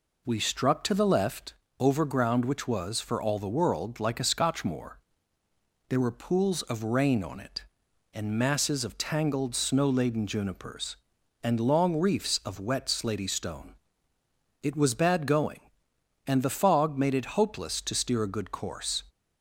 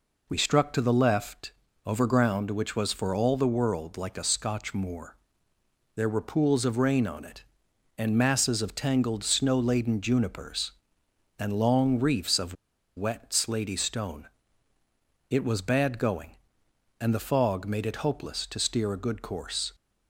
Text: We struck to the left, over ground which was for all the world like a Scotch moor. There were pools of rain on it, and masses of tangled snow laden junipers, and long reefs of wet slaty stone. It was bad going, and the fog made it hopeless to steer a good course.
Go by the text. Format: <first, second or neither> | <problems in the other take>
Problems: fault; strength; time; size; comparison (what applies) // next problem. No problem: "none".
first | pauses between "of" and "wet"; at 12.5 s; 0.42 s long